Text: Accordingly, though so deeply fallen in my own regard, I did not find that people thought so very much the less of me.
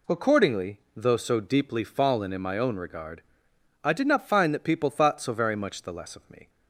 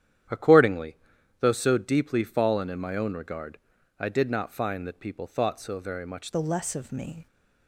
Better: first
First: none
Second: starts louder than the rest; strong; until 1.7 s; 10.5 dB // changes voice at "the"; from 6.3 s on; 0.9 s long

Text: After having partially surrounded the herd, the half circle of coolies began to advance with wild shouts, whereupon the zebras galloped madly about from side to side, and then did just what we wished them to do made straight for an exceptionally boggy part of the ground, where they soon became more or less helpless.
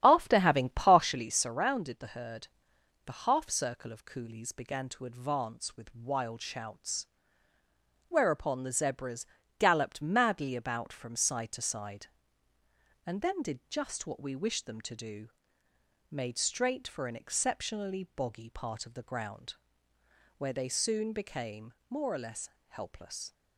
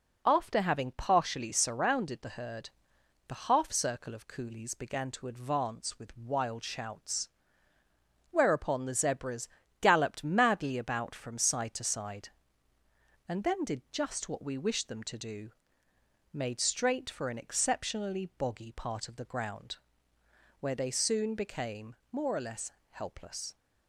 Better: second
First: starts louder than the rest; strong; until 1.3 s; 10.5 dB // pauses between "zebras" and "galloped"; slight; at 9.2 s; 0.32 s long // pauses between "do" and "made"; noticeable; at 15.2 s; 0.82 s long // pauses between "became" and "more"; slight; at 21.7 s; 0.16 s long // pauses between "less" and "helpless"; slight; at 22.4 s; 0.20 s long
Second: pauses between "zebras" and "galloped"; slight; at 9.4 s; 0.32 s long // pauses between "do" and "made"; noticeable; at 15.5 s; 0.82 s long // pauses between "became" and "more"; slight; at 21.9 s; 0.16 s long // pauses between "less" and "helpless"; slight; at 22.7 s; 0.20 s long

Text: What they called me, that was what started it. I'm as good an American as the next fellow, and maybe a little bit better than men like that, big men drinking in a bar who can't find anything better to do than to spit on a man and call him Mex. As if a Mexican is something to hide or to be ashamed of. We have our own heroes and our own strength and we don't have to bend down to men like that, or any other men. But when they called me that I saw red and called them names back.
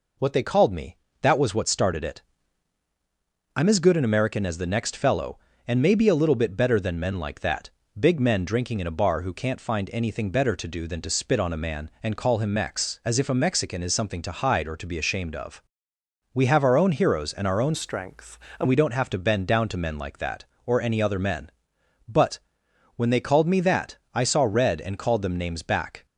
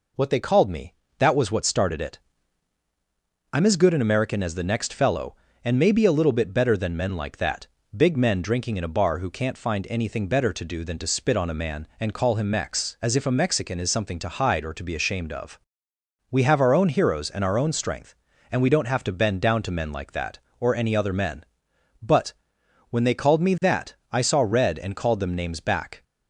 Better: second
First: changes voice from "strength" to "and"; from 17.7 to 18.6 s; 0.9 s long // pauses between "But" and "when"; noticeable; at 22.3 s; 0.58 s long // pauses between "that" and "I"; slight; at 23.9 s; 0.16 s long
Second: pauses between "But" and "when"; noticeable; at 22.3 s; 0.58 s long // pauses between "that" and "I"; slight; at 23.9 s; 0.16 s long

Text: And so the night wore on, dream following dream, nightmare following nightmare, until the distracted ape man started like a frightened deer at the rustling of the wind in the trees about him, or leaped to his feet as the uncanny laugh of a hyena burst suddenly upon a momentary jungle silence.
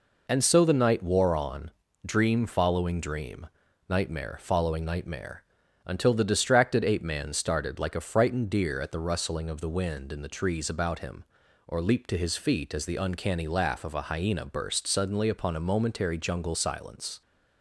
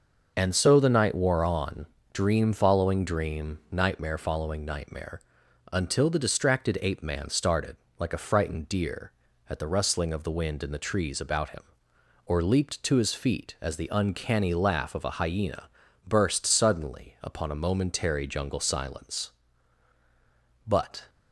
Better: first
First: none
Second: pauses between "started" and "like"; slight; at 7.7 s; 0.24 s long // pauses between "hyena" and "burst"; at 15.6 s; 0.40 s long // goes on to say "But"; slight; from 20.6 s on; 0.42 s long

